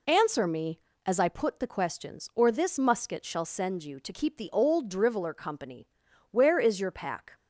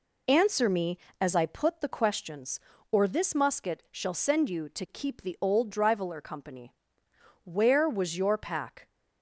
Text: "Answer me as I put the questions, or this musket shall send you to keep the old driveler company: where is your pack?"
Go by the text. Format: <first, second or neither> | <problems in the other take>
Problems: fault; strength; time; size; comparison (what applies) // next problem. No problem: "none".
first | says "was" for "is"; at 7.8 s